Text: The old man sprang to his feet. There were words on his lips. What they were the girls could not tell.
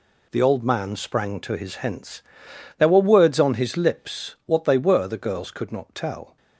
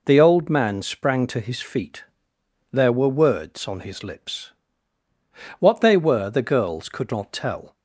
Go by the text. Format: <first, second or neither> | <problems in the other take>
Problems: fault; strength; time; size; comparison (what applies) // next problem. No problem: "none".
second | says "hence" for "feet"; at 1.7 s